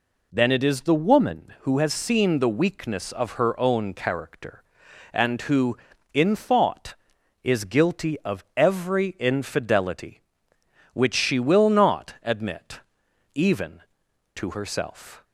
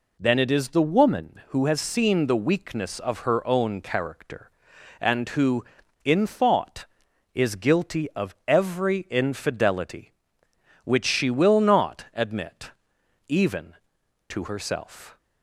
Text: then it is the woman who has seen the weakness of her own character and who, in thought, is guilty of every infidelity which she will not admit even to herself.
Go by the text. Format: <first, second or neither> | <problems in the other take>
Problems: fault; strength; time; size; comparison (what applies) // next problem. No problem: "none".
neither | pauses between "admit" and "even"; noticeable; the same in both